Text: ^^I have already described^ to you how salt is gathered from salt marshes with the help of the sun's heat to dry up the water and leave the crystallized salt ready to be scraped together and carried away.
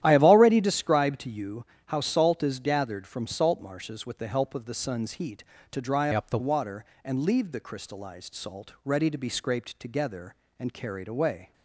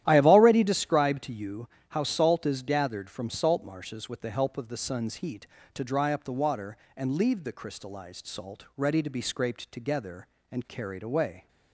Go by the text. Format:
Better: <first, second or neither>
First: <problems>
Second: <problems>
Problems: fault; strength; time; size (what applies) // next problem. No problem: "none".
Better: second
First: starts louder than the rest; strong; until 1.0 s; 12 dB // pauses between "you" and "how"; slight; at 1.6 s; 0.22 s long // changes voice from "up" to "the"; from 6.1 to 6.3 s; 0.2 s long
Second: starts louder than the rest; strong; until 1.0 s; 12 dB // pauses between "you" and "how"; slight; at 1.6 s; 0.22 s long